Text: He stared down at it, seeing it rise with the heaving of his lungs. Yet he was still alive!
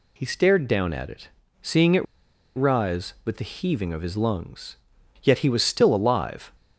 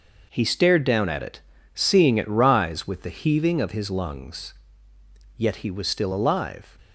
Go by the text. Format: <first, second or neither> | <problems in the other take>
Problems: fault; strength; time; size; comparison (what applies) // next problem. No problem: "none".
second | pauses between "it" and "rise"; noticeable; at 2.0 s; 0.52 s long